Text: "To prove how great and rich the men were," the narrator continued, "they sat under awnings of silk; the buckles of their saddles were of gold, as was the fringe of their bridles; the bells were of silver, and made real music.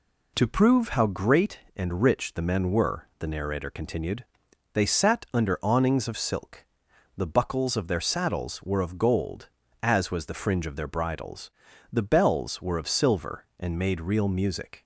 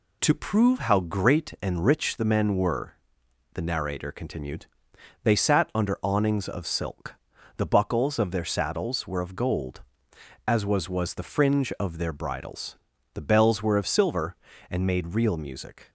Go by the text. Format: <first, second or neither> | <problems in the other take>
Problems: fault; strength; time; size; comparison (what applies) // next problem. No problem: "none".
first | says "was" twice; at 10.8 s